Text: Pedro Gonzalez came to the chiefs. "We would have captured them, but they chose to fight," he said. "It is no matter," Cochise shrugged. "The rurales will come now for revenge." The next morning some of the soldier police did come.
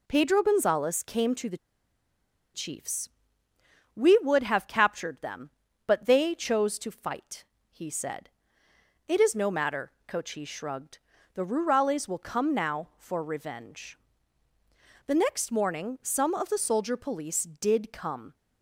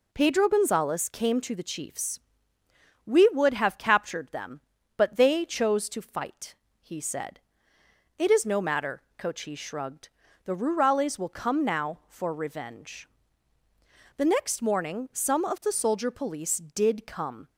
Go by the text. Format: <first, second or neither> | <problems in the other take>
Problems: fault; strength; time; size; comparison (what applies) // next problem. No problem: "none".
second | pauses between "the" and "chiefs"; noticeable; at 1.5 s; 0.96 s long